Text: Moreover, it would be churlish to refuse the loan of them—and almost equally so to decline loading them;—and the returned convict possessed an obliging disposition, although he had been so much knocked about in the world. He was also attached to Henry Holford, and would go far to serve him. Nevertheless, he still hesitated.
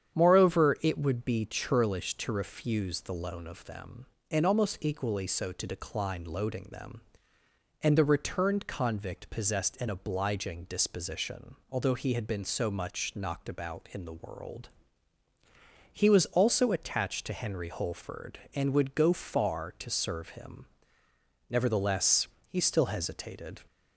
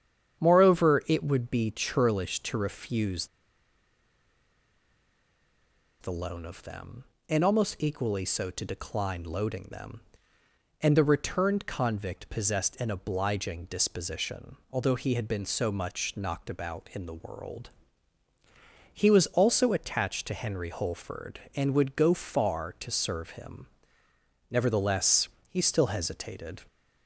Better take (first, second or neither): first